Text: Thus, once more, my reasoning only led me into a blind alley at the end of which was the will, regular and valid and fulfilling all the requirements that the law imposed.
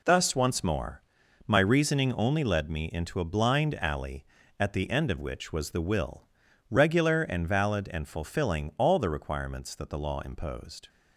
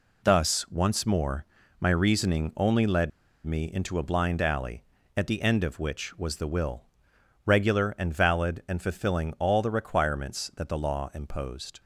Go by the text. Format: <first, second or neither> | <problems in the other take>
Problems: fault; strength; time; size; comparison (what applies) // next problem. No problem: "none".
first | pauses between "led" and "me"; slight; at 3.1 s; 0.36 s long